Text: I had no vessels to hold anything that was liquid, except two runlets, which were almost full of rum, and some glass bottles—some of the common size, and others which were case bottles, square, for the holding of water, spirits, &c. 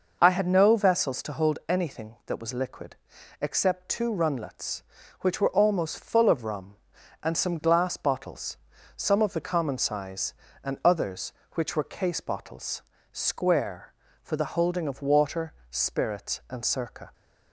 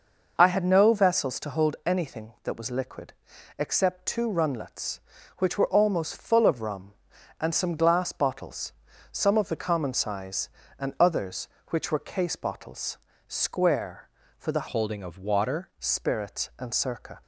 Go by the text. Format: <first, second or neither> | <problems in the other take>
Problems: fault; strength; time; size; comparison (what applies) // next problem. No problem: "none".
first | changes voice from "holding" to "water"; from 14.6 to 15.6 s; 1.0 s long